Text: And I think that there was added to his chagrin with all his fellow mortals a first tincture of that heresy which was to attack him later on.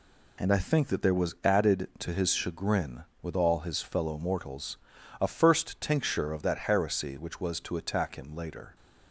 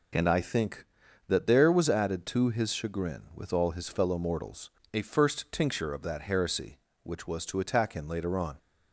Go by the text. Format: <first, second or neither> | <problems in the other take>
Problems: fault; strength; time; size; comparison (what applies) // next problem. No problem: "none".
second | pauses between "mortals" and "a"; at 4.7 s; 0.44 s long; slight in the second // stops before "on"; at 8.7 s